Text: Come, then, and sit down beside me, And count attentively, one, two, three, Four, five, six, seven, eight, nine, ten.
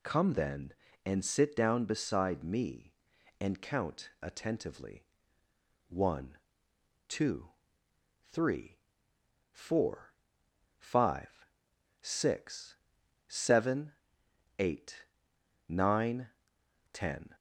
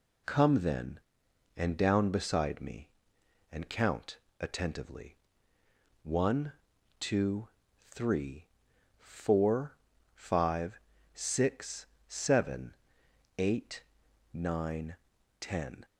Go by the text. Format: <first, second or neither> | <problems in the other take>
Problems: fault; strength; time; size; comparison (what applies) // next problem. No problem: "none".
first | skips "sit"; at 1.7 s // pauses between "count" and "attentively"; slight; at 4.1 s; 0.24 s long